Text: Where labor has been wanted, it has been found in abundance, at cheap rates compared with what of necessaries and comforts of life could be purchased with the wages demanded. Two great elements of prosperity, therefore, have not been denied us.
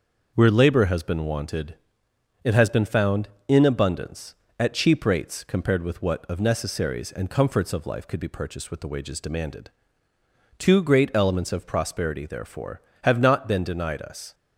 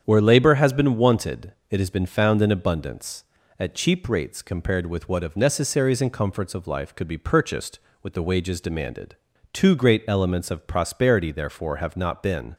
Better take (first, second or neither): first